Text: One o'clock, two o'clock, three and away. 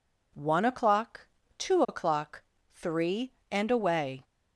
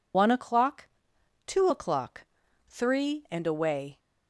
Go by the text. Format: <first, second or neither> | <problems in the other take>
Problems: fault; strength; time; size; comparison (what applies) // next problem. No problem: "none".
first | loses the start of "One"; at 0.1 s; 115 ms